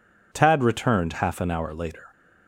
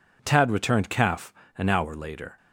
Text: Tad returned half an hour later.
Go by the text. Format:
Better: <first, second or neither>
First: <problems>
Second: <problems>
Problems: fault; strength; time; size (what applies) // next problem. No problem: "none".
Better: first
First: none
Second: says "calf" for "half"; at 0.8 s